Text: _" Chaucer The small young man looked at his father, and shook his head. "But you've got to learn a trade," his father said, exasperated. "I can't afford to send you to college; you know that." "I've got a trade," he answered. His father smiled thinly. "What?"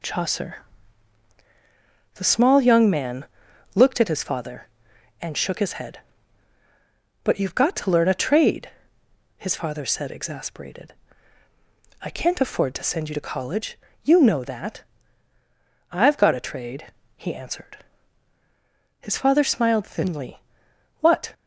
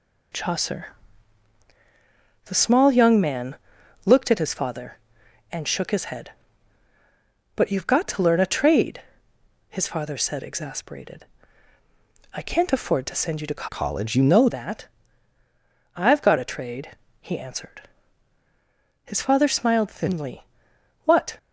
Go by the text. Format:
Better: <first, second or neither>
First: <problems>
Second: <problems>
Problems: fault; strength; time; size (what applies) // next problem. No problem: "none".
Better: first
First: pauses between "Chaucer" and "The"; strong; at 0.6 s; 1.5 s long // pauses between "man" and "looked"; noticeable; at 3.2 s; 0.52 s long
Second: pauses between "Chaucer" and "The"; strong; at 0.9 s; 1.5 s long // pauses between "man" and "looked"; noticeable; at 3.5 s; 0.52 s long // changes voice from "college" to "know"; from 13.6 to 14.4 s; 0.8 s long